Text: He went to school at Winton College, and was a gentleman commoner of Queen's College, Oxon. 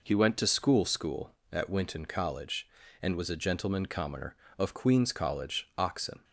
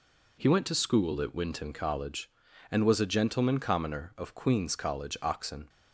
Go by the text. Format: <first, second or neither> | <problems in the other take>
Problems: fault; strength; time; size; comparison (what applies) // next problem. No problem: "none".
second | says "school" twice; at 0.8 s